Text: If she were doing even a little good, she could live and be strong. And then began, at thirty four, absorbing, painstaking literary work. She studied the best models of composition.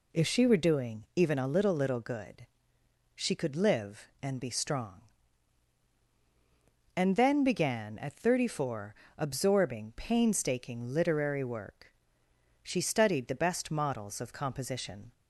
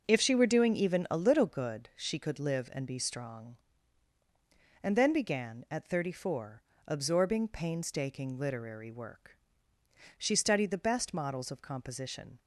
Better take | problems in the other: second | says "little" twice; at 1.7 s

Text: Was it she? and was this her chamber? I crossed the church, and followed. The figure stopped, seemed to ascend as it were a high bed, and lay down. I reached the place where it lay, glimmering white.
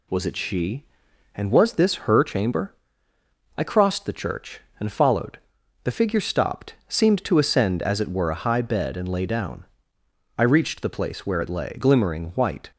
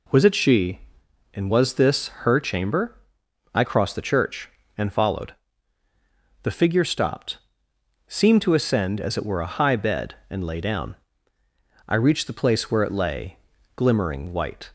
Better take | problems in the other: neither | none

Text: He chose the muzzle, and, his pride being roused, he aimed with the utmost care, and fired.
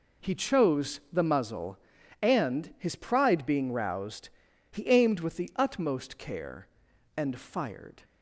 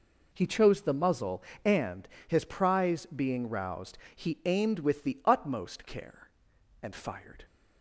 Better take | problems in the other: first | says "prize" for "pride"; at 2.4 s

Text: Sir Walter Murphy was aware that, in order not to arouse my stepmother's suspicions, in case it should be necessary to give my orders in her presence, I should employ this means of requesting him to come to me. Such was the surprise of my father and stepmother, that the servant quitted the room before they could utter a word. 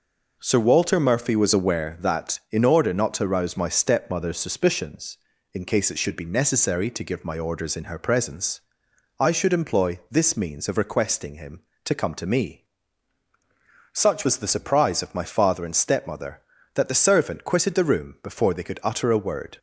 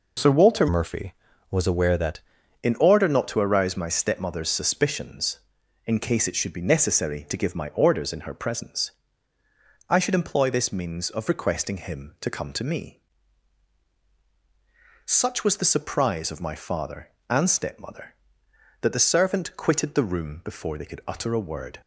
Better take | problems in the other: first | changes voice from "Murphy" to "that"; from 0.6 to 2.2 s; 1.6 s long

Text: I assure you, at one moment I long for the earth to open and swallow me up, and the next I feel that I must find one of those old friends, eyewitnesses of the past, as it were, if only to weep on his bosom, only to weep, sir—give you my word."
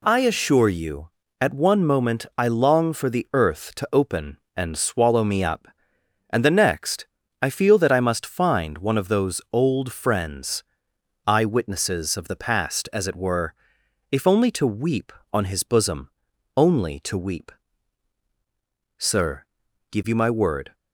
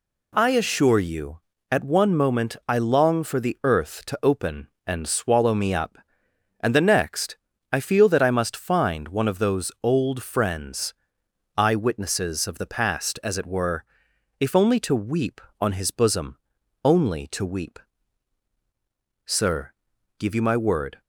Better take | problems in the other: neither | pauses between "next" and "I"; slight; the same in both

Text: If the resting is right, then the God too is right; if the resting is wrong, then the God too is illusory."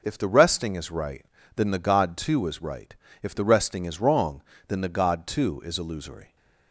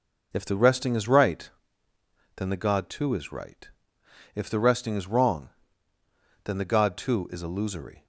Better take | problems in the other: neither | none

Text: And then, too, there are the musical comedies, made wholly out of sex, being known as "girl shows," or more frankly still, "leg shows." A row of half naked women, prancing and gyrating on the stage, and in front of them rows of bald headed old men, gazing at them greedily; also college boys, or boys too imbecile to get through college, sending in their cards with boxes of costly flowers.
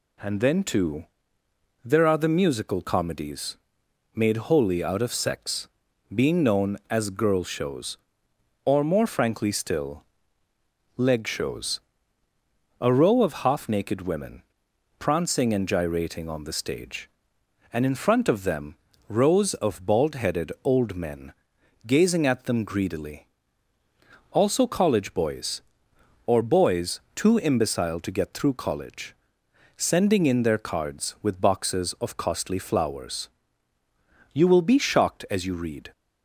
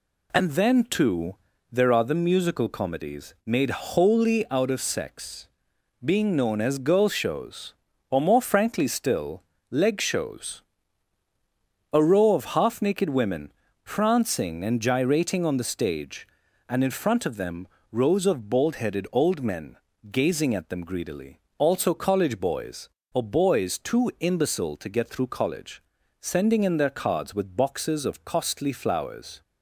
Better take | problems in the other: second | pauses between "them" and "rows"; slight; at 18.7 s; 0.32 s long; slight in the second // goes on to say "You will be shocked as you read"; from 34.3 s on; 1.5 s long

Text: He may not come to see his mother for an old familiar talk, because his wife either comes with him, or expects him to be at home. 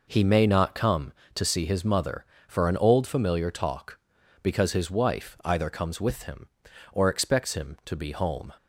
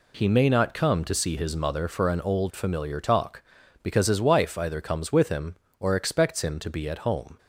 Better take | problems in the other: second | skips "at"; at 8.1 s

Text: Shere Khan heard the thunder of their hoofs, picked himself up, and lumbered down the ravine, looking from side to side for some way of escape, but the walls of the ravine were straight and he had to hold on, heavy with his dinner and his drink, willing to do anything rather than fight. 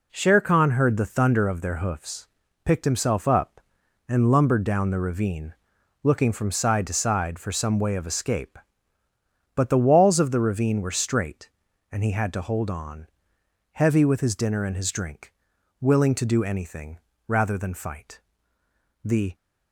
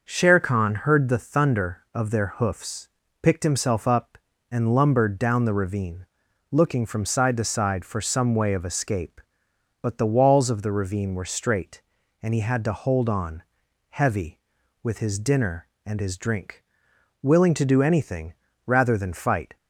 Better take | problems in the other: second | pauses between "anything" and "rather"; slight; at 16.9 s; 0.28 s long; slight in the second // goes on to say "The"; slight; from 19.0 s on; 0.32 s long

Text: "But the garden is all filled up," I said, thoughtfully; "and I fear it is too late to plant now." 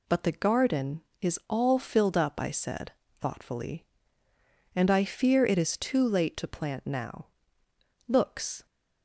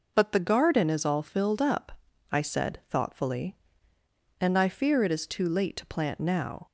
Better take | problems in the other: second | goes on to say "Looks"; from 8.0 s on; 0.58 s long

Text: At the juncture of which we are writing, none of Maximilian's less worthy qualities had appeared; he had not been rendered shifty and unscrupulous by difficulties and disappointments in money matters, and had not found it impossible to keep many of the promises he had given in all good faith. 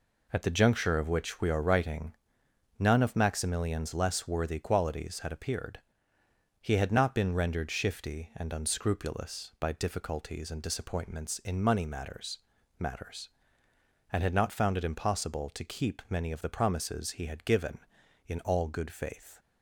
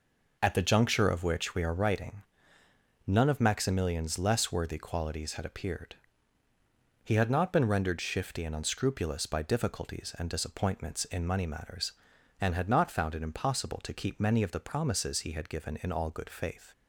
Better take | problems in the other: second | says "matters" twice; at 12.7 s

